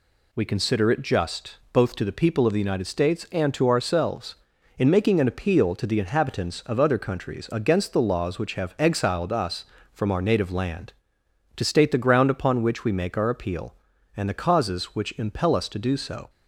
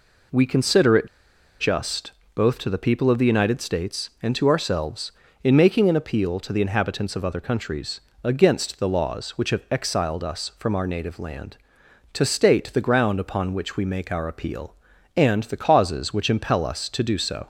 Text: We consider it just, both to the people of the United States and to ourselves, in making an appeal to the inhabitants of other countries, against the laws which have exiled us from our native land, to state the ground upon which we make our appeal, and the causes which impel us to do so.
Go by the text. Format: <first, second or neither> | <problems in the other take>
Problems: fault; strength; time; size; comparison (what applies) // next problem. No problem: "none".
first | pauses between "it" and "just"; noticeable; at 1.0 s; 0.54 s long